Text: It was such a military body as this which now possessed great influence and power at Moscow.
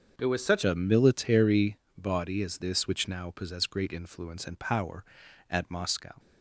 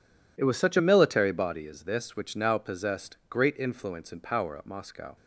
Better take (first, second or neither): second